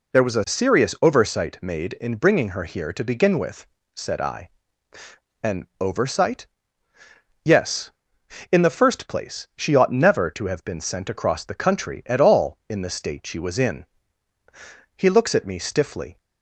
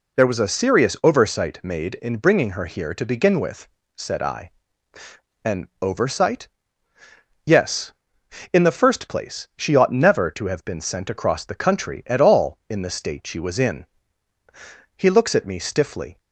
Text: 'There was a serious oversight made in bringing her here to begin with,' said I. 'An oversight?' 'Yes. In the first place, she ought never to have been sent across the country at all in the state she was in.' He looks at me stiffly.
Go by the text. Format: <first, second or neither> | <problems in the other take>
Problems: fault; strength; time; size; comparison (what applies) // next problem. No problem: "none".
neither | pauses between "An" and "oversight"; slight; the same in both